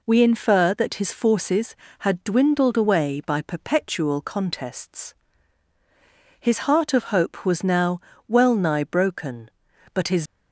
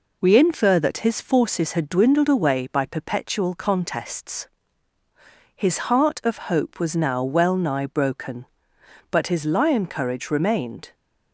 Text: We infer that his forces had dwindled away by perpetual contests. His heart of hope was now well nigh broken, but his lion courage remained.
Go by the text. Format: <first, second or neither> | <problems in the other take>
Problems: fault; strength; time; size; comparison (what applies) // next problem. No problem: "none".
second | pauses between "now" and "well"; slight; at 7.9 s; 0.26 s long // stops before "lion courage remained"; at 10.2 s